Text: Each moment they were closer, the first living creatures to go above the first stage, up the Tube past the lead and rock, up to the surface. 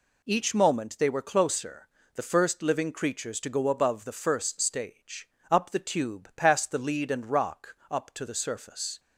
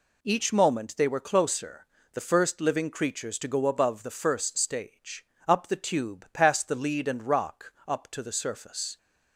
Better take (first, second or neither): neither